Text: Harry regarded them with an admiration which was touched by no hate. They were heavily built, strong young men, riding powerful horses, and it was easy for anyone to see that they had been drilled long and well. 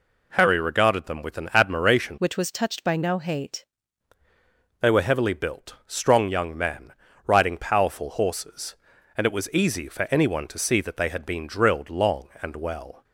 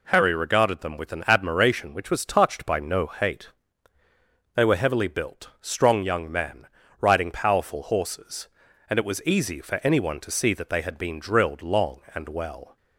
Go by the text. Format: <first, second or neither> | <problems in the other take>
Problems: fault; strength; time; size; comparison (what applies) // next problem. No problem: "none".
second | changes voice from "which" to "hate"; from 2.1 to 3.6 s; 1.5 s long